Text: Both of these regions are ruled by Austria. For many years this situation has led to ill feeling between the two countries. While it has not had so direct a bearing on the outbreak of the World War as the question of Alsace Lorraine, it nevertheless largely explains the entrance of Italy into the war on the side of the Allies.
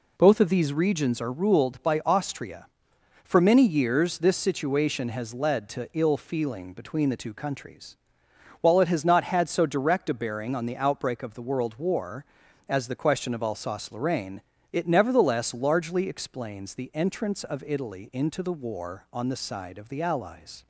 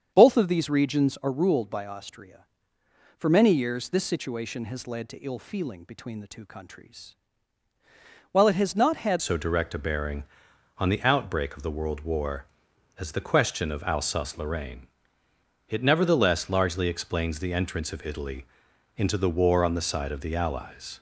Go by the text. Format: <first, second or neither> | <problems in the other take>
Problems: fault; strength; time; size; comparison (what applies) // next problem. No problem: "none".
first | starts louder than the rest; strong; until 1.1 s; 7.5 dB // changes voice at "so"; from 9.2 s on; 11.7 s long // pauses between "Italy" and "into"; noticeable; at 18.4 s; 0.54 s long